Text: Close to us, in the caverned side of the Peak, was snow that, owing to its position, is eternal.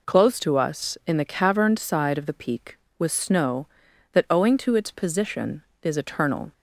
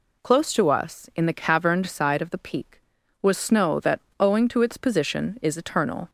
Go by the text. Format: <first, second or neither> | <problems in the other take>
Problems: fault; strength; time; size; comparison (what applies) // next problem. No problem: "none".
neither | none